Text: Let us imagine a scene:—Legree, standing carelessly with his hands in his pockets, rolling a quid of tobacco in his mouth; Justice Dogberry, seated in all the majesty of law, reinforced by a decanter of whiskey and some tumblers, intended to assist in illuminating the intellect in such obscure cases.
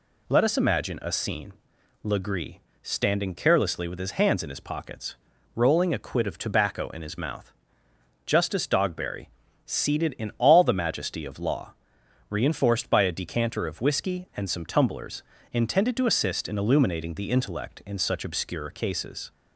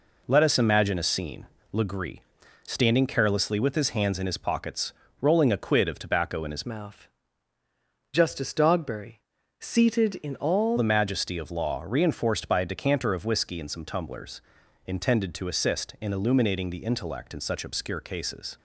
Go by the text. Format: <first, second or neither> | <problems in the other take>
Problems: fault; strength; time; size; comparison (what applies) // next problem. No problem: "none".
first | changes voice from "mouth" to "all"; from 6.6 to 10.7 s; 4.1 s long